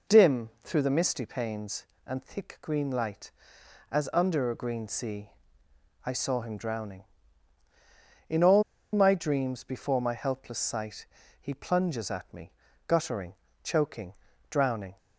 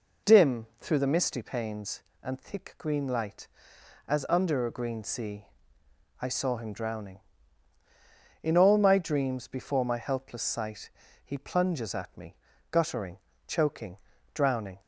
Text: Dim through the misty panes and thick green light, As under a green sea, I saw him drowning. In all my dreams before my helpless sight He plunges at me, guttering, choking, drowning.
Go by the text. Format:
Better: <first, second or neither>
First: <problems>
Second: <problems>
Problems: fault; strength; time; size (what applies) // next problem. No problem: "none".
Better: second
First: pauses between "all" and "my"; slight; at 8.6 s; 0.30 s long // pauses between "sight" and "He"; slight; at 11.0 s; 0.34 s long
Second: pauses between "sight" and "He"; slight; at 10.9 s; 0.34 s long